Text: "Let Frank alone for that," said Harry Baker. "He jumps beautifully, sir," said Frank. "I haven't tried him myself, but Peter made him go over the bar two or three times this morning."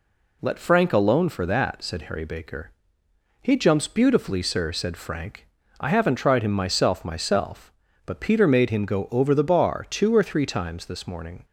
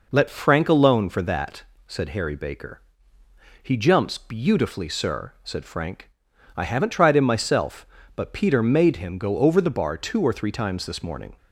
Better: second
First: says "myself" twice; at 7.0 s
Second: none

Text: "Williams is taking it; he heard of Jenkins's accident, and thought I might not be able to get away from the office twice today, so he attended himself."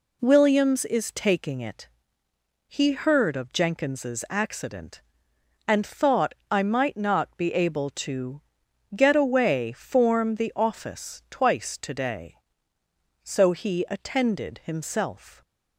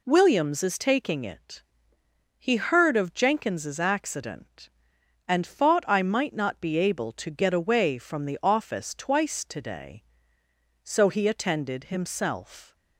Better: second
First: pauses between "thought" and "I"; slight; at 6.3 s; 0.18 s long // pauses between "to" and "get"; noticeable; at 8.4 s; 0.52 s long // says "form" for "from"; at 9.7 s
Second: none

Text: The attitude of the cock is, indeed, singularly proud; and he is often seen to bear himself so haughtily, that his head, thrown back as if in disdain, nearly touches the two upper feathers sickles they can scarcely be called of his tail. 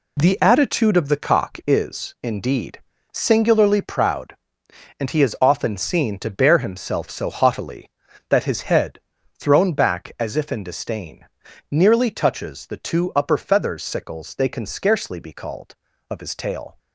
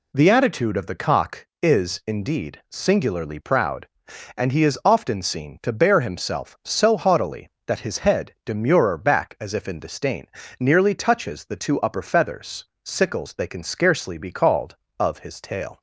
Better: first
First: none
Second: says "demurer" for "thrown"; at 8.4 s // pauses between "feathers" and "sickles"; slight; at 12.6 s; 0.18 s long

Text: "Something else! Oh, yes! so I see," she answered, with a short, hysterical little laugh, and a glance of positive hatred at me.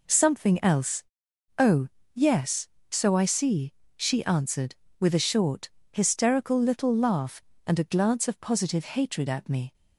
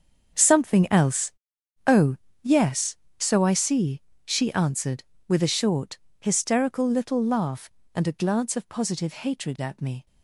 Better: first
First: none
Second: gets quieter; strong; throughout; 14 dB

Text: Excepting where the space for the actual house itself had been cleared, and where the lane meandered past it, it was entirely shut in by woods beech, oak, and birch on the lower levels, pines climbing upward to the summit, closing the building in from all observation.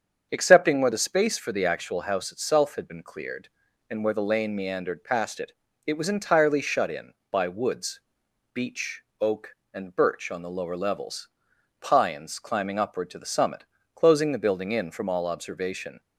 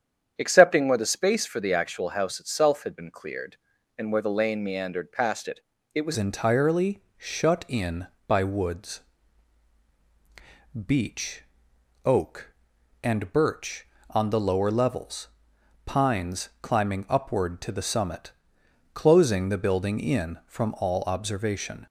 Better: first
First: starts louder than the rest; until 1.3 s; 7 dB // pauses between "woods" and "beech"; noticeable; at 8.0 s; 0.52 s long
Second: starts louder than the rest; strong; until 1.3 s; 8.5 dB // changes voice at "entirely"; from 6.1 s on; 15.7 s long // pauses between "entirely" and "shut"; slight; at 7.0 s; 0.16 s long // pauses between "woods" and "beech"; strong; at 9.0 s; 1.8 s long

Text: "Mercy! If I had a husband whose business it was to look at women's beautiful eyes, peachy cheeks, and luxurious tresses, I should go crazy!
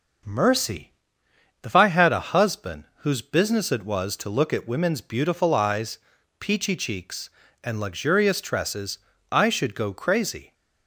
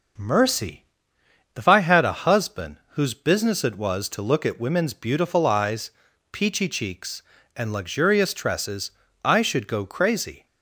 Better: neither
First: pauses between "husband" and "whose"; slight; at 2.8 s; 0.16 s long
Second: pauses between "husband" and "whose"; slight; at 2.7 s; 0.16 s long

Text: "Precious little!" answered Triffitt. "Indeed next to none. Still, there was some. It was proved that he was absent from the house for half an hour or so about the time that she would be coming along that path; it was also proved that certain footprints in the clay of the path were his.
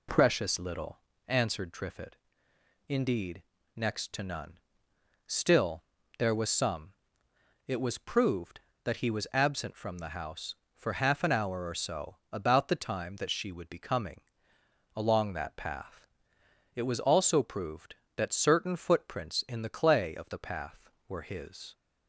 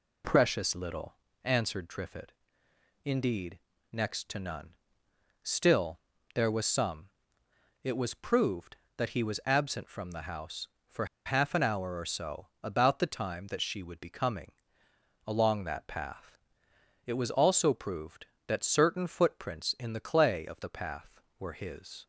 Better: first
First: pauses between "Indeed" and "next"; slight; at 3.4 s; 0.32 s long // pauses between "coming" and "along"; noticeable; at 14.2 s; 0.74 s long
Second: pauses between "Indeed" and "next"; slight; at 3.5 s; 0.32 s long // pauses between "for" and "half"; slight; at 11.0 s; 0.20 s long // pauses between "coming" and "along"; noticeable; at 14.5 s; 0.74 s long

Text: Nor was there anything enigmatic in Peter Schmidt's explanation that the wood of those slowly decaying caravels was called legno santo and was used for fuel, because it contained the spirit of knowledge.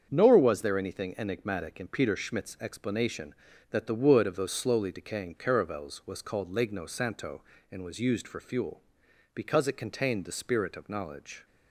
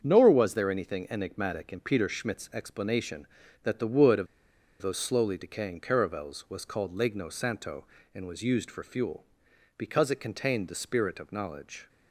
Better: first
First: starts louder than the rest; strong; until 1.1 s; 7 dB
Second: starts louder than the rest; strong; until 1.0 s; 7 dB // pauses between "of" and "those"; noticeable; at 4.2 s; 0.55 s long

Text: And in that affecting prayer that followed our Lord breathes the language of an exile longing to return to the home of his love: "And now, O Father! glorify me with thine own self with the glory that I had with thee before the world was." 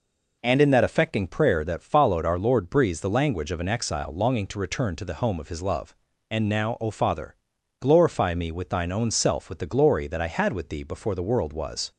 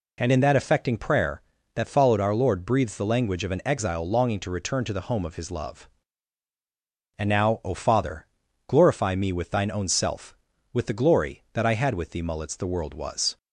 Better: first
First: none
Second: says "mullets" for "before"; at 12.2 s

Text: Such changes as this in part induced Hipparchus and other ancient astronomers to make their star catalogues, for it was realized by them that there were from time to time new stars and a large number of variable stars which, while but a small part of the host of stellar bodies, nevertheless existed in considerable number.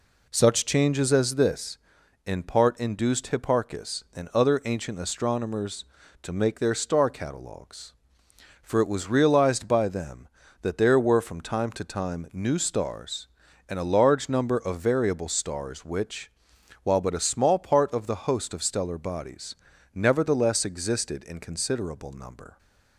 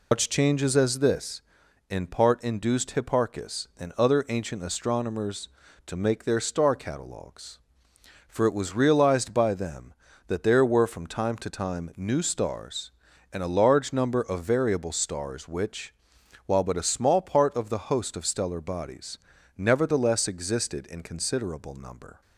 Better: first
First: none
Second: loses the start of "Such"; at 0.1 s; 175 ms

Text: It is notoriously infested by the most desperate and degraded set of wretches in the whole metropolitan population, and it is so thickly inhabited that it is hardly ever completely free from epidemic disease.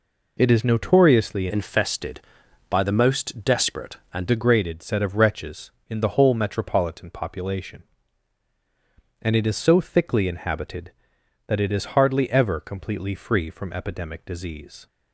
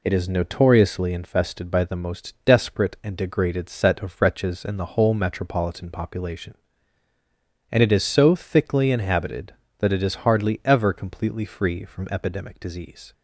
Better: second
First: changes voice from "infested" to "and"; from 1.5 to 4.2 s; 2.7 s long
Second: none

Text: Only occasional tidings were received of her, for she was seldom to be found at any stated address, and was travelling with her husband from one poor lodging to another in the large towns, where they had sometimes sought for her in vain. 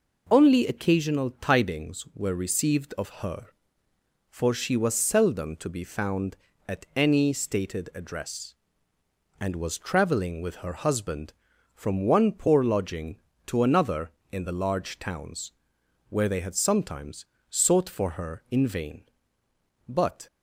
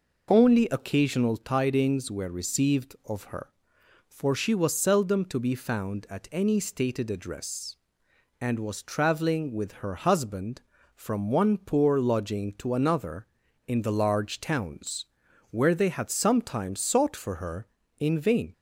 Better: second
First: pauses between "sometimes" and "sought"; slight; at 17.2 s; 0.24 s long // goes on to say "But"; slight; from 19.8 s on; 0.40 s long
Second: none

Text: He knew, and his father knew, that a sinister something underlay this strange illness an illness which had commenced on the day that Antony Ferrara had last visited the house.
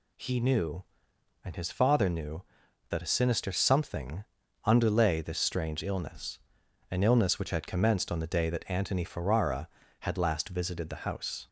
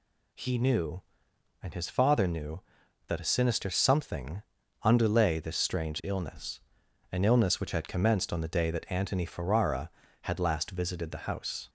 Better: neither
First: pauses between "something" and "underlay"; at 4.2 s; 0.40 s long // pauses between "illness" and "an"; noticeable; at 6.3 s; 0.52 s long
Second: pauses between "something" and "underlay"; at 4.4 s; 0.40 s long // pauses between "illness" and "an"; noticeable; at 6.5 s; 0.52 s long

